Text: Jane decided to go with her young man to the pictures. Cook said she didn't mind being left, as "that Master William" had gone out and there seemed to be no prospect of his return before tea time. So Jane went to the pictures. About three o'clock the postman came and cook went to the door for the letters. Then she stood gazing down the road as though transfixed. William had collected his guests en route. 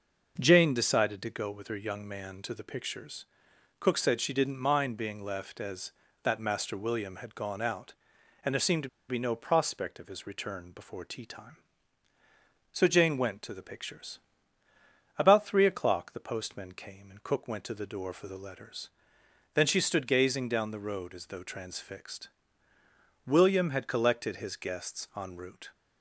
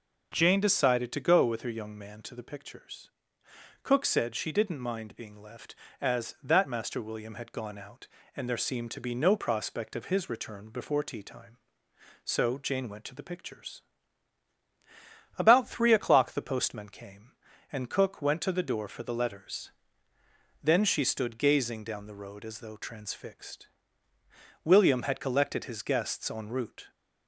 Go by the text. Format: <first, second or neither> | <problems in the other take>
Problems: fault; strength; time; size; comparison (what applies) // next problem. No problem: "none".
second | pauses between "to" and "be"; slight; at 8.8 s; 0.20 s long